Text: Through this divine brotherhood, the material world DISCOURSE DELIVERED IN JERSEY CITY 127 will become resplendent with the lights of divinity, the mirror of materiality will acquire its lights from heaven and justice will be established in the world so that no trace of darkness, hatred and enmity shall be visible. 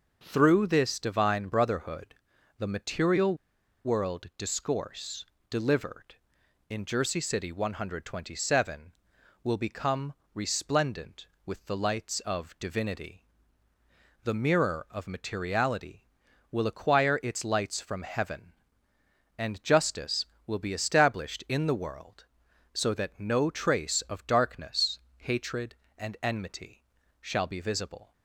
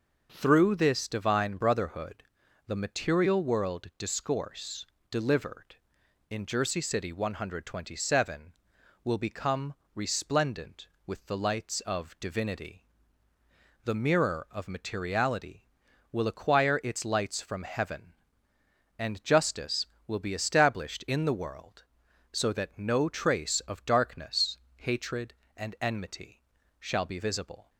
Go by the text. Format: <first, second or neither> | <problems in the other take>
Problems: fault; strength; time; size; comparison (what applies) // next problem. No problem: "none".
second | pauses between "material" and "world"; noticeable; at 3.3 s; 0.50 s long // pauses between "DISCOURSE" and "DELIVERED"; slight; at 5.2 s; 0.24 s long; slight in the second // pauses between "become" and "resplendent"; slight; at 10.1 s; 0.18 s long; slight in the second // pauses between "enmity" and "shall"; slight; at 26.8 s; 0.36 s long; slight in the second